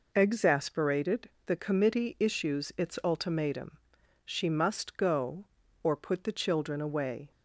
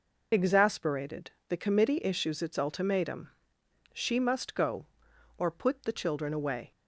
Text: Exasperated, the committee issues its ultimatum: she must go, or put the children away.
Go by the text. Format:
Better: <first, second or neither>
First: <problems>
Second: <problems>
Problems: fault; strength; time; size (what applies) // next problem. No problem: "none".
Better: first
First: none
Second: loses the start of "Exasperated"; at 0.3 s; 35 ms